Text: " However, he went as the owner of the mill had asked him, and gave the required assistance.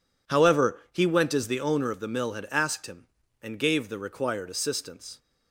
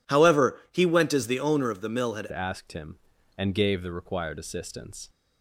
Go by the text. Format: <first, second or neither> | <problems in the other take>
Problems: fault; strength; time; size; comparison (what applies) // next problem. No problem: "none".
first | changes voice at "asked"; from 2.3 s on; 2.7 s long